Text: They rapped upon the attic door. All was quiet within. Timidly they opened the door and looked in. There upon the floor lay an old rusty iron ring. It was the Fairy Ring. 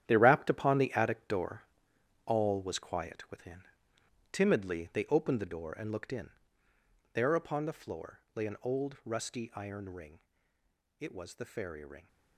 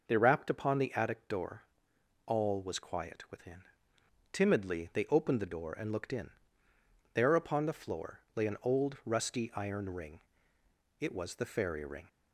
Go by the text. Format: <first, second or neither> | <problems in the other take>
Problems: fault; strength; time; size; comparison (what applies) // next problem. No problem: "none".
second | gets quieter; strong; throughout; 11 dB // pauses between "floor" and "lay"; slight; at 8.1 s; 0.16 s long; slight in the second